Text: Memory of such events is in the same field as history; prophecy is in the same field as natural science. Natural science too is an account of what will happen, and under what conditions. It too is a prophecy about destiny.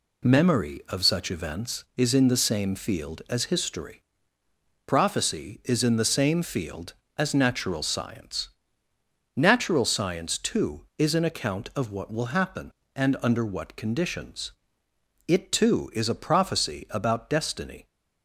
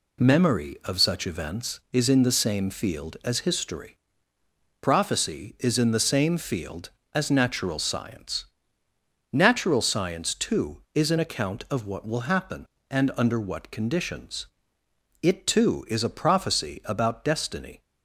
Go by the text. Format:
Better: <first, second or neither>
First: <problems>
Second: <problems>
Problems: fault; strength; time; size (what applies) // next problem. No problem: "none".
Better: neither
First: none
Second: none